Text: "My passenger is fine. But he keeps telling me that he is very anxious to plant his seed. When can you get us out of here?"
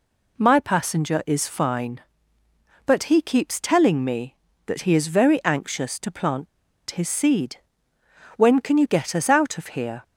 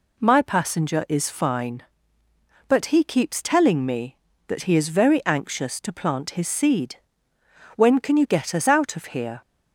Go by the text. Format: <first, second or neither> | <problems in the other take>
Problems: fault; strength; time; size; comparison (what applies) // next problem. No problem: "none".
second | pauses between "plant" and "his"; at 6.4 s; 0.44 s long